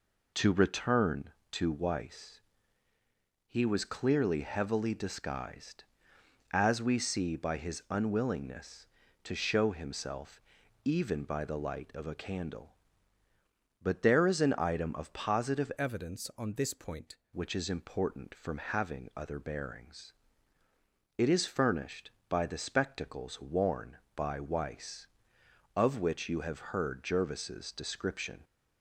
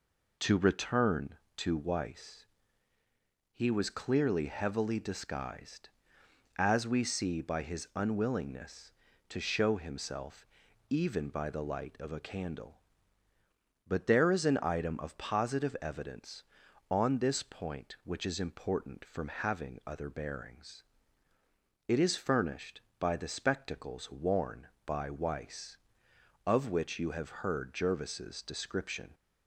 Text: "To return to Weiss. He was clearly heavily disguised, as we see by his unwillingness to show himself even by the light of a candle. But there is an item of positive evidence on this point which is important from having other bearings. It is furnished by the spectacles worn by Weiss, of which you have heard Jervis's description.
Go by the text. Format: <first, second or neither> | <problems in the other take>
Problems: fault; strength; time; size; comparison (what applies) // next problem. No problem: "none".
second | pauses between "himself" and "even"; at 10.4 s; 0.44 s long; also in the second // changes voice from "evidence" to "point"; from 15.7 to 17.1 s; 1.4 s long